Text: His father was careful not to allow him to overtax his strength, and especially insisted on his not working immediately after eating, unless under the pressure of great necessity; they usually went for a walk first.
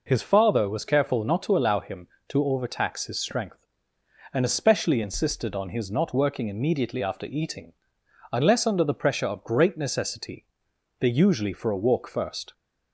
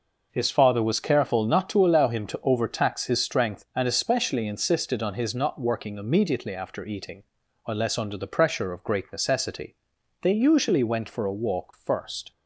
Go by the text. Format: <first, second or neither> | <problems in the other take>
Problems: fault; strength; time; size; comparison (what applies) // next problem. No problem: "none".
second | skips "went"; at 11.5 s